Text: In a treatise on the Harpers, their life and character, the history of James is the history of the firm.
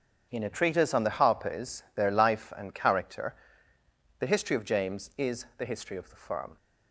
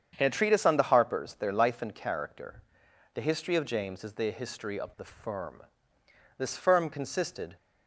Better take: first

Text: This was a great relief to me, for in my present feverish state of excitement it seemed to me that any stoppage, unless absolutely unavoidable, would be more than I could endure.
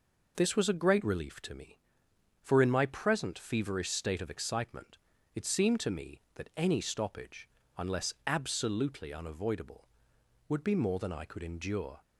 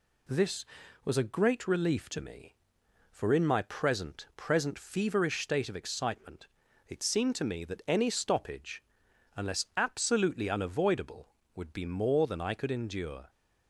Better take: first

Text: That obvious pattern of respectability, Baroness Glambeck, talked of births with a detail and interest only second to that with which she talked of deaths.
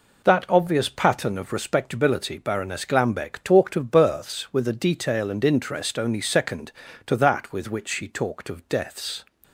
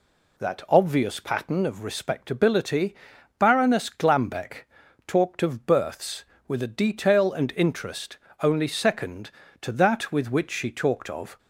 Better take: first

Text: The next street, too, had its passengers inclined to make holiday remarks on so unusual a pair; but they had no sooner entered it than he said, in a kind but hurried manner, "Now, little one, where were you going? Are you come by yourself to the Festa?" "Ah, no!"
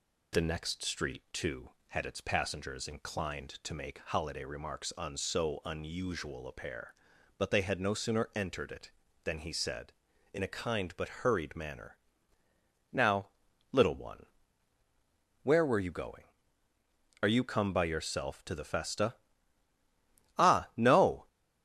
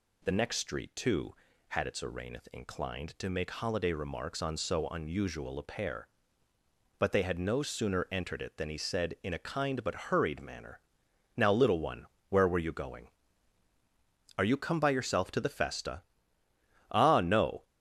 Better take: first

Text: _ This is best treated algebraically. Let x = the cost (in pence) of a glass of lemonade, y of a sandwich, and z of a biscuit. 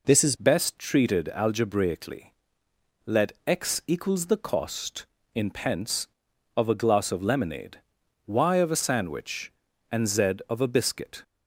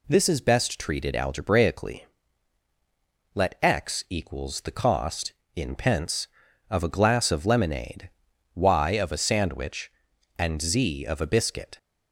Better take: second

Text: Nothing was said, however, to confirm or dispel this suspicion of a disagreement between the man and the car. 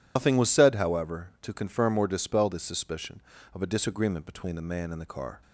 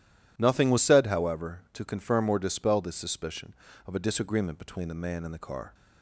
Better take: second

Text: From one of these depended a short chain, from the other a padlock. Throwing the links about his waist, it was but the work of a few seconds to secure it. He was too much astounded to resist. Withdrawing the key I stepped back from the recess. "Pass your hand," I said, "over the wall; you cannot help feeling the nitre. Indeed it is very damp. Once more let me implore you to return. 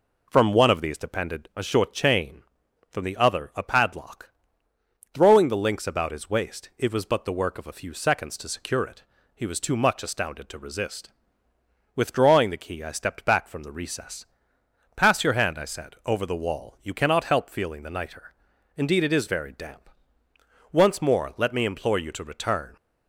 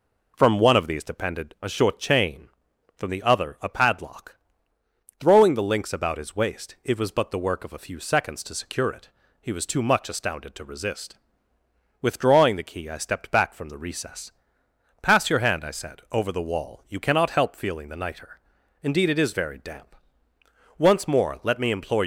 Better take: first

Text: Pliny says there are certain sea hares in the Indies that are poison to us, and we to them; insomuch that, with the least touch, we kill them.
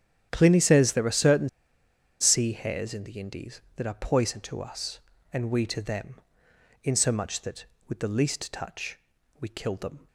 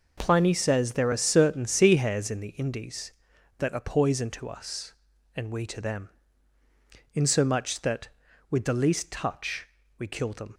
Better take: second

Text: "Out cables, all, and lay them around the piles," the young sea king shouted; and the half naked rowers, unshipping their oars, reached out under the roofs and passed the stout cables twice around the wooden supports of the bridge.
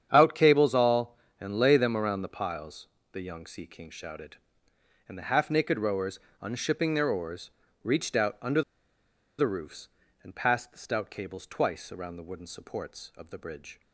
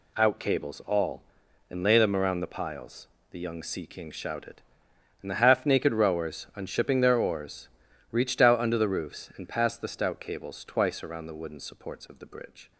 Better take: second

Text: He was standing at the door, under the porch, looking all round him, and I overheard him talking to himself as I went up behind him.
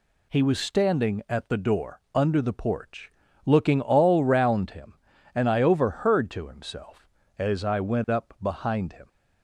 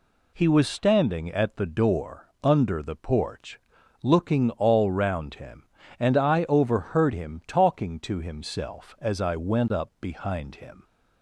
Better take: second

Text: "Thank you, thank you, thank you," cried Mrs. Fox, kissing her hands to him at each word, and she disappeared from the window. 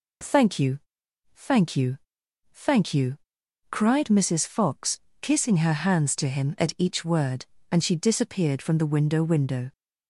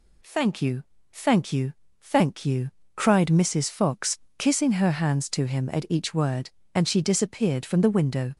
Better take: second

